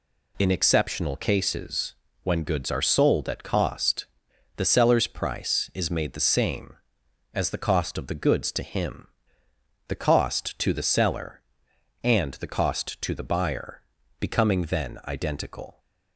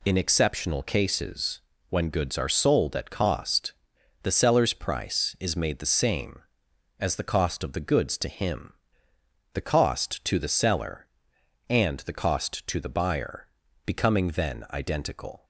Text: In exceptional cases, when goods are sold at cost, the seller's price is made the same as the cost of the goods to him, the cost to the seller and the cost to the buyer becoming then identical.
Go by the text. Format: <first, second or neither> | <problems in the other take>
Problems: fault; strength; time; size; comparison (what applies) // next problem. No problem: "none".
neither | pauses between "buyer" and "becoming"; the same in both